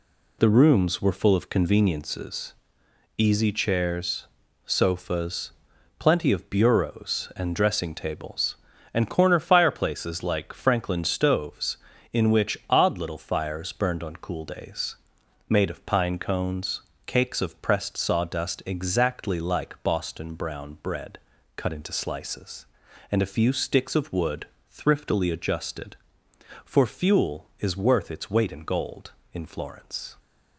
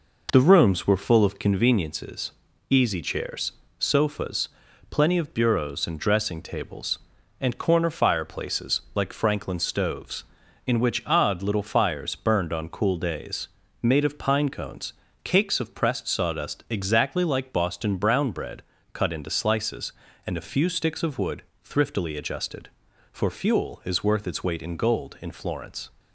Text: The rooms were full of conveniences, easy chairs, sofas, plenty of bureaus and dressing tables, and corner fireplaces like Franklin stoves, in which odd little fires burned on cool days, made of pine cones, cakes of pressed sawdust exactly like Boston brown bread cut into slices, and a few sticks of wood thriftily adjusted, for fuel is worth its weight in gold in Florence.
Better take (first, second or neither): first